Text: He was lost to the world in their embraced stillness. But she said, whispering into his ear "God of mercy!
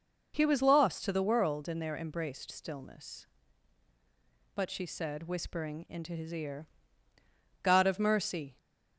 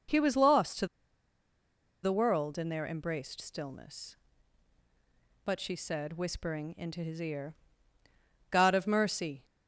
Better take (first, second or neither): first